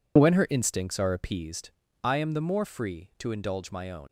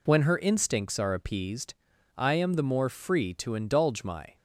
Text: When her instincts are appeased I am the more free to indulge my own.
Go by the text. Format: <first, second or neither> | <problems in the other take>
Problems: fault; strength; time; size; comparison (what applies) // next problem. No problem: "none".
first | pauses between "appeased" and "I"; at 1.7 s; 0.42 s long; slight in the first // stops before "own"; at 4.3 s